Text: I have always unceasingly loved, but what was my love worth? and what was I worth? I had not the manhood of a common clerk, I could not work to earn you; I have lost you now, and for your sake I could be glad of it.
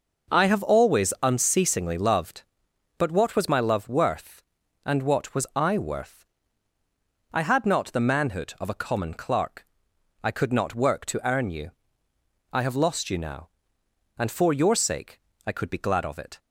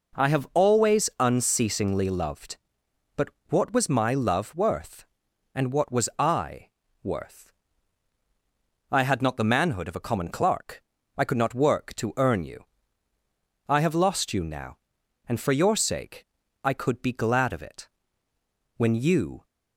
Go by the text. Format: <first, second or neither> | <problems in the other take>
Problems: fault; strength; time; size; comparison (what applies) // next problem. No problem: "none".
first | pauses between "but" and "what"; slight; at 3.2 s; 0.20 s long // pauses between "I" and "worth"; slight; at 6.6 s; 0.34 s long // pauses between "sake" and "I"; at 16.2 s; 0.38 s long; slight in the first // goes on to say "When you"; noticeable; from 18.7 s on; 0.68 s long